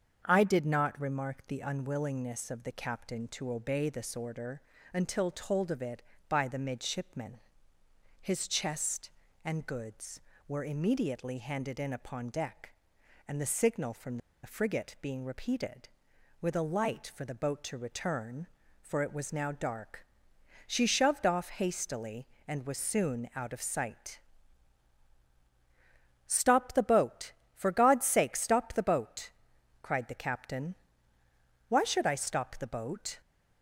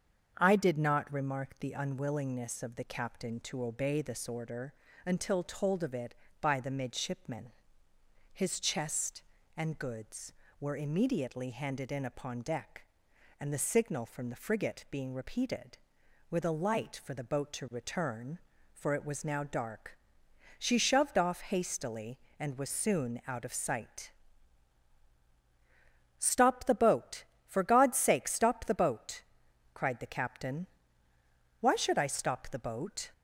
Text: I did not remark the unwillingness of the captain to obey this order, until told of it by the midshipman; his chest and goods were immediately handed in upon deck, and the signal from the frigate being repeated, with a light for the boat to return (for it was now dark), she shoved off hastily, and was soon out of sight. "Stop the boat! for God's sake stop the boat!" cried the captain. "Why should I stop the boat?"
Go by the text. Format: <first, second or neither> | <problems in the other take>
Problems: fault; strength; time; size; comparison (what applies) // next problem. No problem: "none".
second | starts louder than the rest; until 1.2 s; 7 dB; also in the second // pauses between "from" and "the"; slight; at 14.1 s; 0.26 s long